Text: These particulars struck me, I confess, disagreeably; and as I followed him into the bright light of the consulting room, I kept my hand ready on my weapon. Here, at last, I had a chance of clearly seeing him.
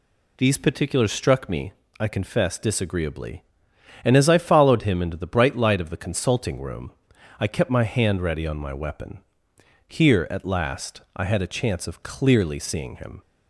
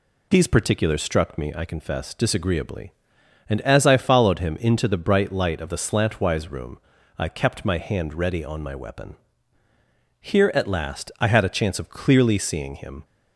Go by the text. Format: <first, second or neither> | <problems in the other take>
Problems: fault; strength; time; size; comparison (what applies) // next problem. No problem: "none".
first | says "slantwise" for "consulting"; at 5.7 s